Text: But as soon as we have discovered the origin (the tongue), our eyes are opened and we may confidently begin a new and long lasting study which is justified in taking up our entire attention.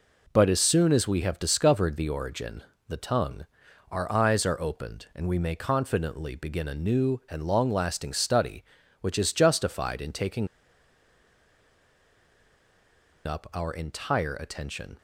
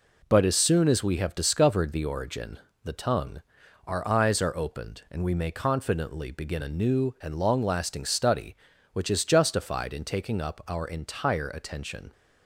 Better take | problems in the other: second | pauses between "taking" and "up"; strong; at 10.4 s; 2.7 s long

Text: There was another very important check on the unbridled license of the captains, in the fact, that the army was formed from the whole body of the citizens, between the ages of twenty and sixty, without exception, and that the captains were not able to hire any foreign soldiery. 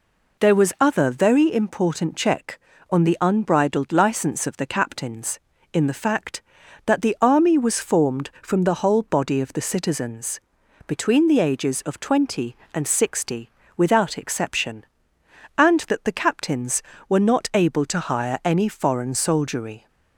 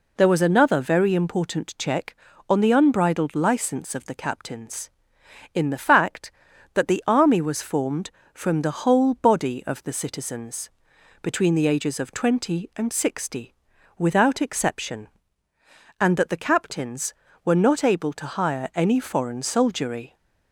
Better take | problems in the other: second | says "other" for "another"; at 0.7 s

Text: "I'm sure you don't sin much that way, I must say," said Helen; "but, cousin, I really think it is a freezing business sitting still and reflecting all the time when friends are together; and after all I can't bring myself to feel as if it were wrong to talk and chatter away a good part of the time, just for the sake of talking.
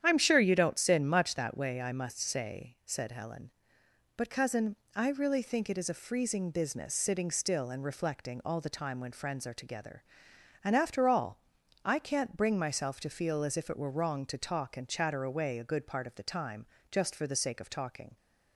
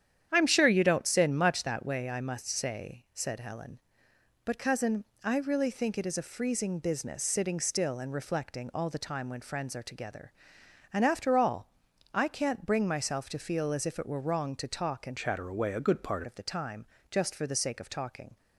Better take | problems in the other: first | starts louder than the rest; strong; until 1.3 s; 9.5 dB; strong in the first // pauses between "all" and "I"; at 11.6 s; 0.44 s long; also in the first // changes voice from "chatter" to "part"; from 15.1 to 16.2 s; 1.1 s long

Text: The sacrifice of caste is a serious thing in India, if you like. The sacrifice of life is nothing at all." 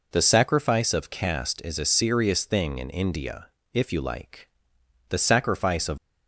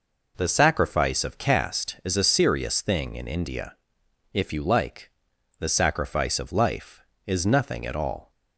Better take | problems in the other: second | stops before "life is nothing at all"; at 5.9 s

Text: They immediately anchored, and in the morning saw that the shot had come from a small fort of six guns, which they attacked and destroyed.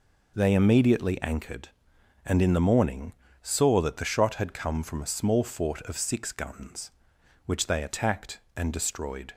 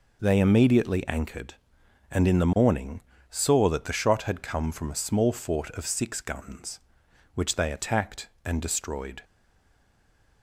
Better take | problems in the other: first | pauses between "morning" and "saw"; slight; at 3.0 s; 0.28 s long; slight in the first // stays silent after the last word; noticeable; from 9.2 s on; 1.2 s long

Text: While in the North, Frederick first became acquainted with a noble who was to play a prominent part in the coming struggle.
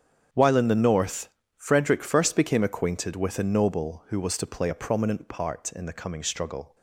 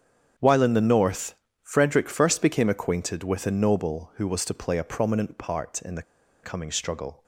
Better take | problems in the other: first | starts louder than the rest; strong; until 1.6 s; 8 dB; strong in the first // pauses between "the" and "coming"; at 6.0 s; 0.40 s long

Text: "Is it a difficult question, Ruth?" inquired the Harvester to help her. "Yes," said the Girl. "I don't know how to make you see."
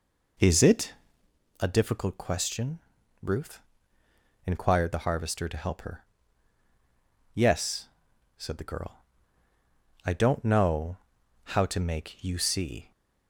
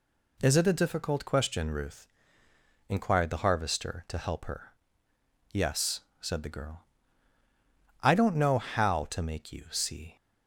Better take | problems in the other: second | starts louder than the rest; noticeable; until 1.3 s; 4.5 dB // pauses between "it" and "a"; noticeable; at 0.9 s; 0.68 s long // pauses between "know" and "how"; noticeable; at 10.9 s; 0.48 s long

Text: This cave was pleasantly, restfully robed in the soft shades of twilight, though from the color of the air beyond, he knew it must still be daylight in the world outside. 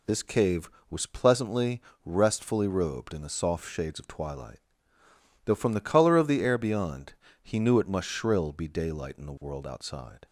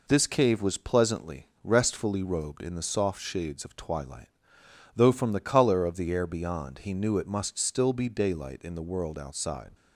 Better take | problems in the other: second | says "shrill" for "still"; at 8.0 s

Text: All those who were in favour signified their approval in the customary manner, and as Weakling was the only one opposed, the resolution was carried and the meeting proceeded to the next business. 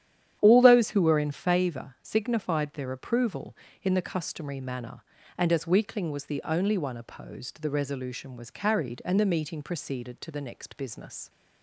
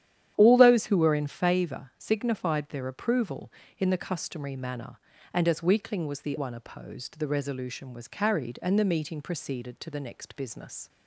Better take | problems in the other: first | starts louder than the rest; strong; until 1.3 s; 10.5 dB; strong in the first // skips "only"; at 6.3 s

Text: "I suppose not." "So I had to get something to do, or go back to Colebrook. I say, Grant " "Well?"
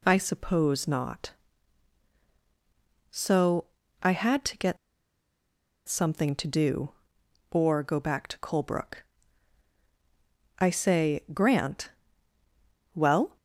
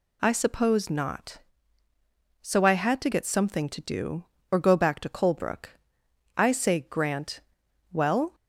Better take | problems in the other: second | pauses between "So" and "I"; slight; at 3.6 s; 0.36 s long // pauses between "get" and "something"; at 4.7 s; 1.1 s long

